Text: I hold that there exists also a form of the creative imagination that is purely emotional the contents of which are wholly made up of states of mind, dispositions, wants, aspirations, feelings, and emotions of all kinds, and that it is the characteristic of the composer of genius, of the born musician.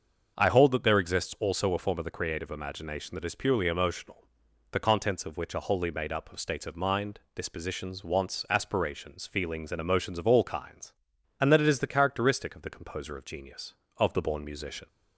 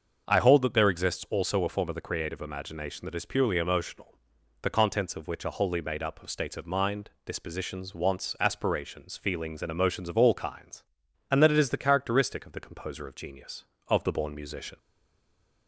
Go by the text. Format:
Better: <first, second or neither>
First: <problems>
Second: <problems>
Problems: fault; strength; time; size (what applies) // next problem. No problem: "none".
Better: first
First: starts louder than the rest; until 1.4 s; 6.5 dB // pauses between "emotional" and "the"; noticeable; at 4.2 s; 0.48 s long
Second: starts louder than the rest; until 1.3 s; 6.5 dB // pauses between "emotional" and "the"; noticeable; at 4.1 s; 0.48 s long // stays silent after the last word; slight; from 14.7 s on; 0.9 s long